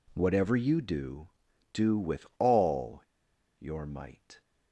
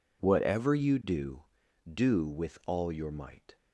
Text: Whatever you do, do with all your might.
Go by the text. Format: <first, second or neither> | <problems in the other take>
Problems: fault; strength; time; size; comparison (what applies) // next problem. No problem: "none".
second | pauses between "all" and "your"; noticeable; at 3.0 s; 0.55 s long